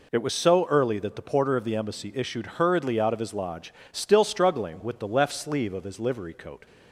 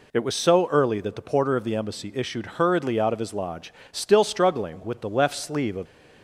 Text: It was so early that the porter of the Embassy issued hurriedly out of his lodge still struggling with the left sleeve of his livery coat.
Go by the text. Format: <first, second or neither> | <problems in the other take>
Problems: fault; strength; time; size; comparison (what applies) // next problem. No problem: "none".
first | pauses between "lodge" and "still"; slight; at 3.7 s; 0.20 s long; slight in the first // stops before "his livery coat"; at 5.8 s